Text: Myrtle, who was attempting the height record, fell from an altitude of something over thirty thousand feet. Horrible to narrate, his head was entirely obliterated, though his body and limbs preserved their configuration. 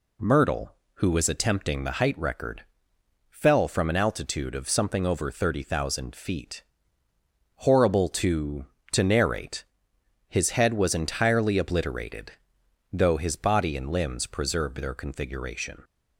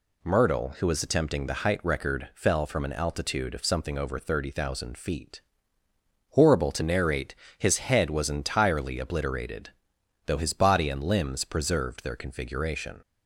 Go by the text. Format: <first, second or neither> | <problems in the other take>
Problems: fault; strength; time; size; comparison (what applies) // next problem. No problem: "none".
second | says "to" twice; at 8.9 s